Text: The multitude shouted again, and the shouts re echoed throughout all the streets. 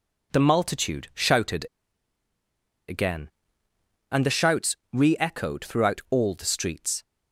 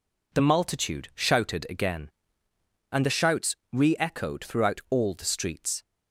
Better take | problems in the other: second | pauses between "shouted" and "again"; at 1.6 s; 1.2 s long // pauses between "shouts" and "re"; slight; at 4.7 s; 0.16 s long; slight in the second

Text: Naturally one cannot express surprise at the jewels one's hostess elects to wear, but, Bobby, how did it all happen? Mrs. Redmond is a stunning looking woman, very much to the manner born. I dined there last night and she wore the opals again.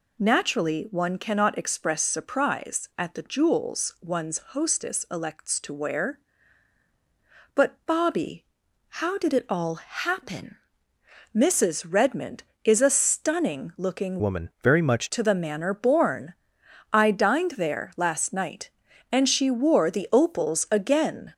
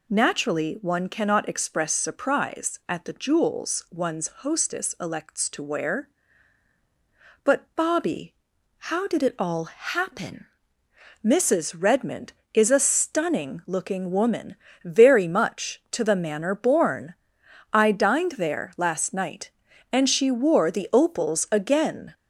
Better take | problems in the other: second | changes voice from "woman" to "much"; from 14.1 to 15.0 s; 0.9 s long

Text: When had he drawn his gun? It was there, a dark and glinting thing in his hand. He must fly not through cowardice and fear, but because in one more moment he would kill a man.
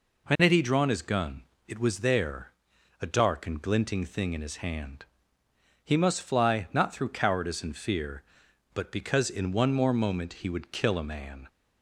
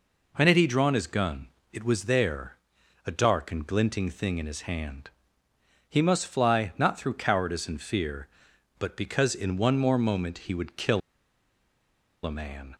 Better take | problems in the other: first | pauses between "kill" and "a"; strong; at 11.0 s; 1.2 s long

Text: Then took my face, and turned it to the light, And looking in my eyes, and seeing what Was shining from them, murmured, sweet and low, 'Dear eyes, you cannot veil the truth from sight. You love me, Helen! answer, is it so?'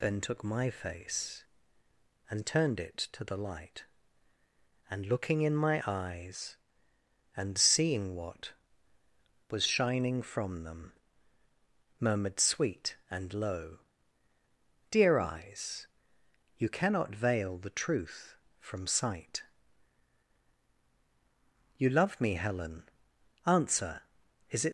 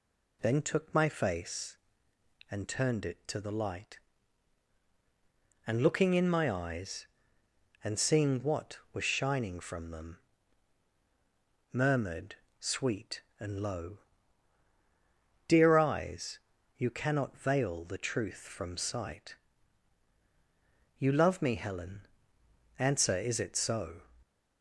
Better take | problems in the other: second | stops before "so"; at 24.6 s

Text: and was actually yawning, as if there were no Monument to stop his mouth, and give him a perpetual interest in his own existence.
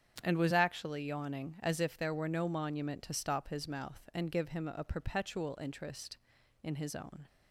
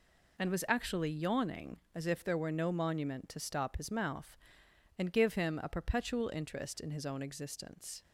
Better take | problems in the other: second | starts louder than the rest; strong; until 1.2 s; 8 dB // stops before "existence"; at 7.2 s

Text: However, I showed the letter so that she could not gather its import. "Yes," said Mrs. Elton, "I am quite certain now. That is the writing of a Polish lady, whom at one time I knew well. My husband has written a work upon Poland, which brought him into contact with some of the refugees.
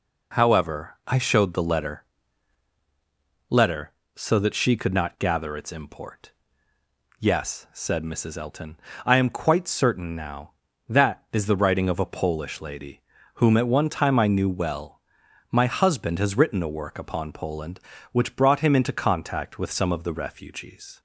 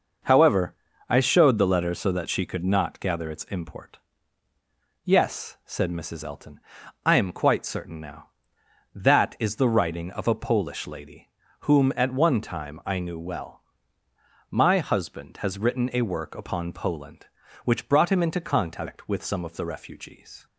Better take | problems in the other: second | says "letter" twice; at 3.5 s

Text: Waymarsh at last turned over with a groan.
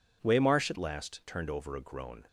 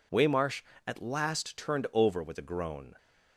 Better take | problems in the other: second | skips "with"; at 1.7 s

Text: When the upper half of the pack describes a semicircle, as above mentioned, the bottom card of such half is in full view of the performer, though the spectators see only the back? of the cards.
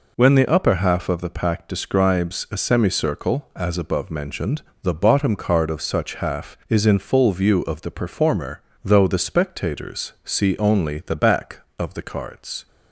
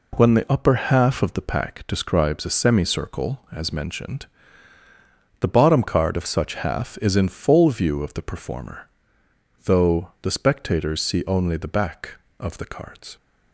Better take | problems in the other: first | skips "above"; at 3.7 s

